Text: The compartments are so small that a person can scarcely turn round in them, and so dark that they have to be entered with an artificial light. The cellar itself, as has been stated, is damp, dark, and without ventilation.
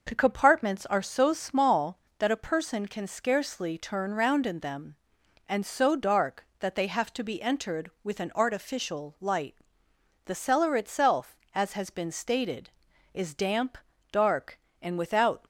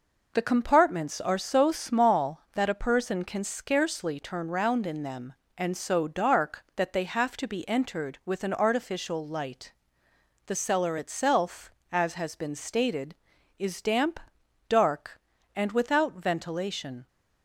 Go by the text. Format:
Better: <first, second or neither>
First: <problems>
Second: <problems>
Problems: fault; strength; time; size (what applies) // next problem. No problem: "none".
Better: second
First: stops before "ventilation"; at 15.4 s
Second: none